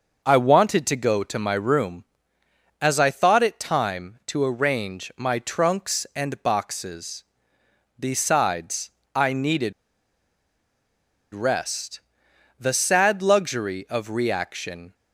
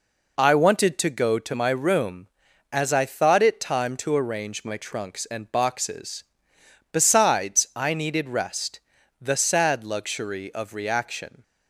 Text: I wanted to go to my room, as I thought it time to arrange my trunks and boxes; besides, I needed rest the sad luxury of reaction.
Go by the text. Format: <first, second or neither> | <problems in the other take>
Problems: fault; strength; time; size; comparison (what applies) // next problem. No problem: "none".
second | pauses between "needed" and "rest"; strong; at 9.7 s; 1.6 s long // pauses between "rest" and "the"; noticeable; at 11.9 s; 0.60 s long; also in the second